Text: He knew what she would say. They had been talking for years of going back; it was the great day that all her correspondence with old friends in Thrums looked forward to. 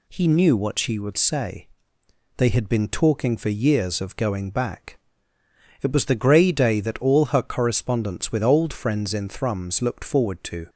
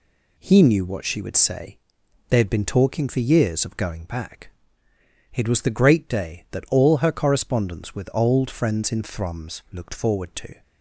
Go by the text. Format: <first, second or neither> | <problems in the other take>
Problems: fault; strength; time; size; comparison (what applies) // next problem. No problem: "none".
second | says "grey" for "great"; at 6.1 s